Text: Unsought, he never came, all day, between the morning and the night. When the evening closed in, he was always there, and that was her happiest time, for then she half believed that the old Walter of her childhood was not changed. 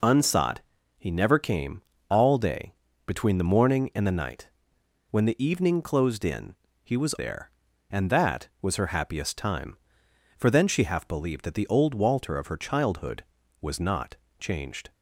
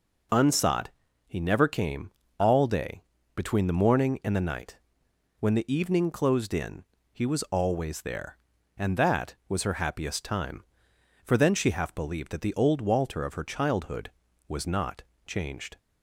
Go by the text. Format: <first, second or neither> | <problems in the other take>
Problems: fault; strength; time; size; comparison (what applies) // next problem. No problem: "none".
second | skips "always"; at 7.1 s // pauses between "not" and "changed"; slight; at 14.1 s; 0.24 s long; slight in the second